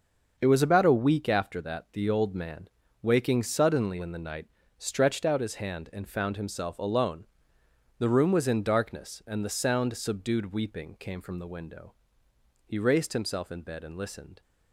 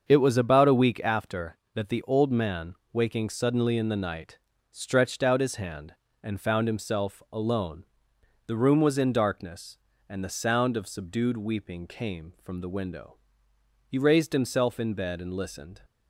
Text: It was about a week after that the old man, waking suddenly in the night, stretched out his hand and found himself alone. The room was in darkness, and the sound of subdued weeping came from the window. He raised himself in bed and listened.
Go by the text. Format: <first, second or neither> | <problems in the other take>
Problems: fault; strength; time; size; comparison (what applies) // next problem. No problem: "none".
second | starts louder than the rest; until 1.3 s; 6.5 dB; also in the second // skips "of"; at 9.9 s